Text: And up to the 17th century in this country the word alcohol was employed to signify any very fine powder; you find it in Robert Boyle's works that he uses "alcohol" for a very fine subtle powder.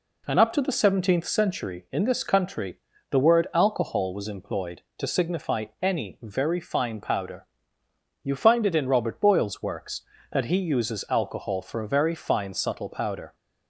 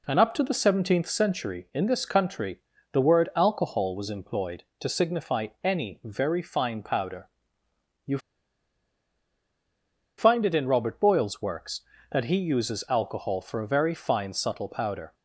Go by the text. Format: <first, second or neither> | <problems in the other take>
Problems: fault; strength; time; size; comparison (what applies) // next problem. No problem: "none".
first | pauses between "country" and "the"; slight; at 2.5 s; 0.34 s long; slight in the first // pauses between "signify" and "any"; slight; at 5.4 s; 0.18 s long; slight in the first // pauses between "you" and "find"; strong; at 8.1 s; 1.9 s long